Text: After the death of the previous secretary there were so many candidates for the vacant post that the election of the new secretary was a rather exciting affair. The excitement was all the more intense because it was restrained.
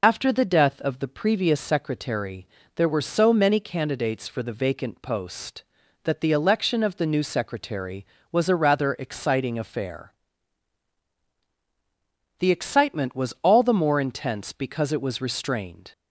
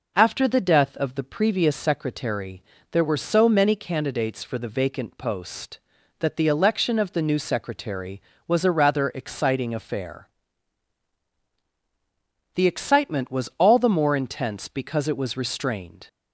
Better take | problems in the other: second | loses the start of "After"; at 0.0 s; 35 ms // pauses between "secretary" and "there"; slight; at 2.4 s; 0.28 s long; slight in the second

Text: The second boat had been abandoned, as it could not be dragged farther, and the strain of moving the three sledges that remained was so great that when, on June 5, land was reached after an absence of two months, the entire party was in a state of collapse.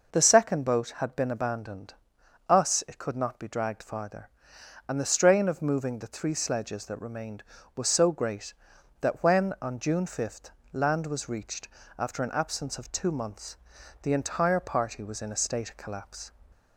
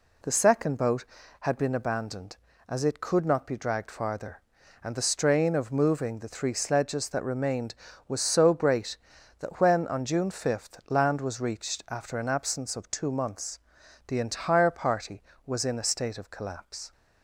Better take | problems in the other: second | says "us" for "as"; at 2.4 s // pauses between "reached" and "after"; slight; at 11.6 s; 0.30 s long

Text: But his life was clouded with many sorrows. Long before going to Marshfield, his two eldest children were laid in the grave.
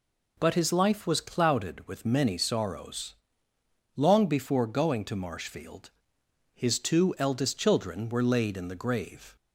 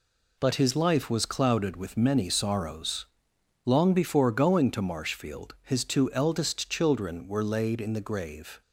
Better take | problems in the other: neither | none

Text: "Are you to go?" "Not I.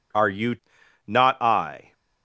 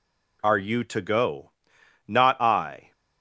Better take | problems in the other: second | skips "to go"; at 0.8 s

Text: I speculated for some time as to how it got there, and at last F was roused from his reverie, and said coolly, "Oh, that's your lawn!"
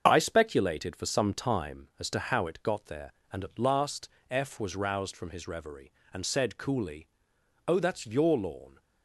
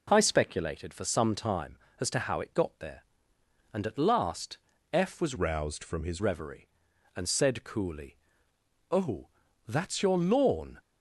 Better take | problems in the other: first | pauses between "last" and "F"; slight; at 4.5 s; 0.34 s long; slight in the first // changes voice from "roused" to "his"; from 5.3 to 6.2 s; 0.9 s long

